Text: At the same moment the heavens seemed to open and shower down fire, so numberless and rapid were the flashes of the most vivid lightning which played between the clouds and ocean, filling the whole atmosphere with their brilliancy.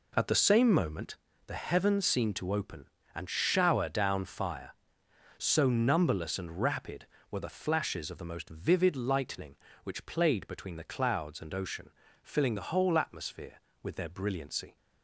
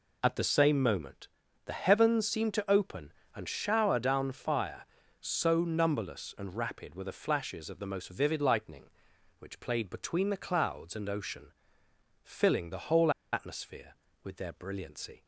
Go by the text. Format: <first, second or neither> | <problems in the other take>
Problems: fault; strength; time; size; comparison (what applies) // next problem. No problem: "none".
first | pauses between "moment" and "the"; slight; at 1.2 s; 0.36 s long; slight in the first // pauses between "whole" and "atmosphere"; slight; at 13.1 s; 0.22 s long